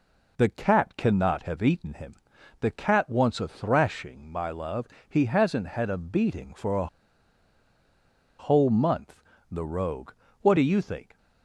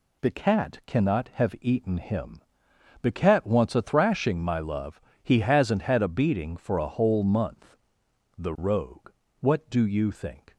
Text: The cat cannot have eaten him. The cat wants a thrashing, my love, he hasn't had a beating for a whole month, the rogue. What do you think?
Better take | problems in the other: second | pauses between "a" and "whole"; strong; at 6.8 s; 1.5 s long

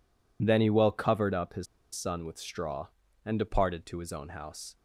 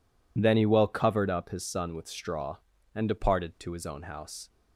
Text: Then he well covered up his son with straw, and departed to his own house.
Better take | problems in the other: second | pauses between "his" and "son"; slight; at 1.6 s; 0.29 s long

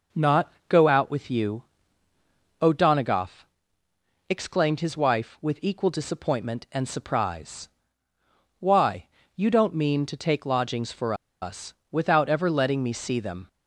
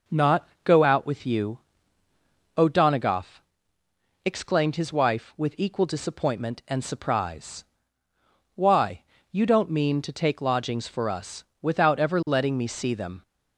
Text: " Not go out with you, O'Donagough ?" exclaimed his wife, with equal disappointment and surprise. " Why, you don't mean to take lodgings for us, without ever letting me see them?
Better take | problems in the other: second | pauses between "Not" and "go"; slight; at 0.5 s; 0.16 s long; slight in the second // pauses between "for" and "us"; slight; at 11.1 s; 0.27 s long

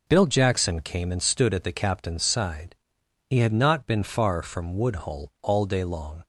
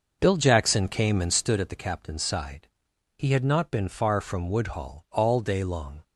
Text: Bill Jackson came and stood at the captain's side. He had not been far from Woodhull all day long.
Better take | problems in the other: first | starts louder than the rest; noticeable; until 1.5 s; 6 dB

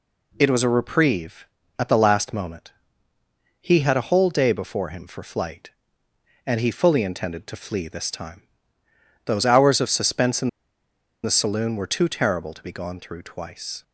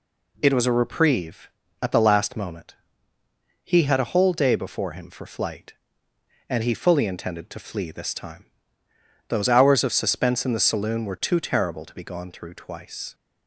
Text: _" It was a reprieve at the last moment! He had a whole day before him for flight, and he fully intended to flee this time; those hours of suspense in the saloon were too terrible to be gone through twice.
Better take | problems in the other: second | pauses between "in" and "the"; noticeable; at 10.4 s; 0.75 s long

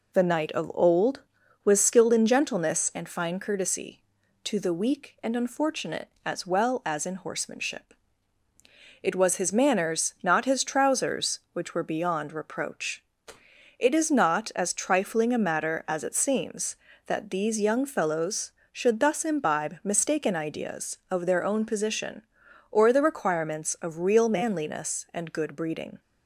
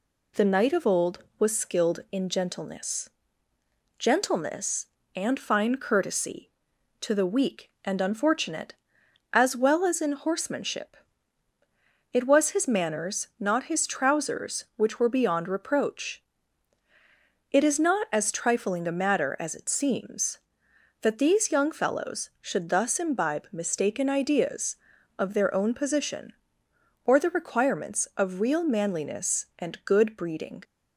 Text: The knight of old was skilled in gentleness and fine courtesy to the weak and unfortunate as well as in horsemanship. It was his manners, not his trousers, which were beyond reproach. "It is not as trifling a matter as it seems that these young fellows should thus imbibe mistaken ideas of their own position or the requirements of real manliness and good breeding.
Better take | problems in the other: first | says "gentleness" twice; at 3.9 s

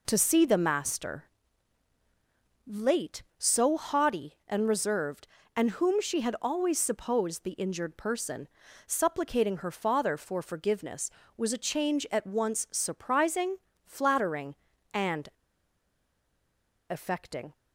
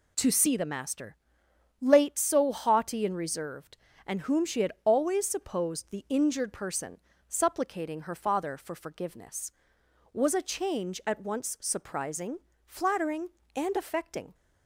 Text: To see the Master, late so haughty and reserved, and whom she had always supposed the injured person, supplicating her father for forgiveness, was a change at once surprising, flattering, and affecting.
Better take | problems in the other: second | pauses between "and" and "affecting"; strong; at 15.2 s; 1.6 s long

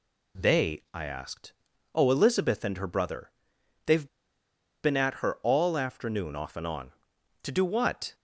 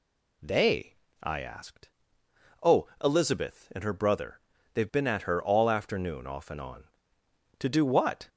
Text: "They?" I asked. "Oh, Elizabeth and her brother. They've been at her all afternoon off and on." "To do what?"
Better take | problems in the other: second | pauses between "They've" and "been"; noticeable; at 4.0 s; 0.77 s long

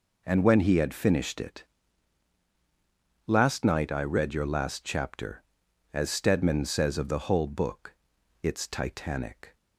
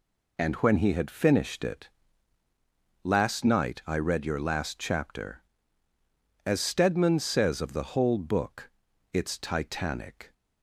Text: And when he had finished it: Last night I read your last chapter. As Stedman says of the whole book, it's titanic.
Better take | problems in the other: neither | none

